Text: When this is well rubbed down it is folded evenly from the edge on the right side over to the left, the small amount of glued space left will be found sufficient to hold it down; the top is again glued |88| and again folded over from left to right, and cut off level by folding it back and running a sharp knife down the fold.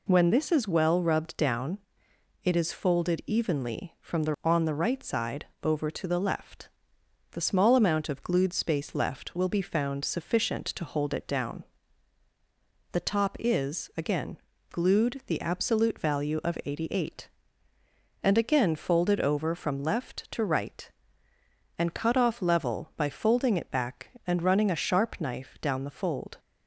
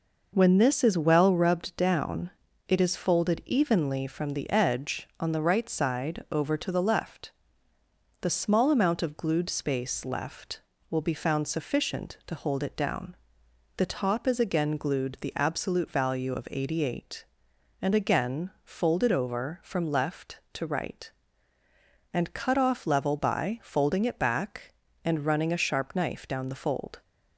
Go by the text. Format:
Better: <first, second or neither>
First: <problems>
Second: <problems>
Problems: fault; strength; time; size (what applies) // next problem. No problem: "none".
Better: second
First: pauses between "down" and "it"; noticeable; at 1.7 s; 0.62 s long // skips "edge"; at 4.3 s // pauses between "side" and "over"; slight; at 5.4 s; 0.16 s long // pauses between "again" and "glued"; slight; at 14.3 s; 0.34 s long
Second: pauses between "down" and "it"; slight; at 2.3 s; 0.36 s long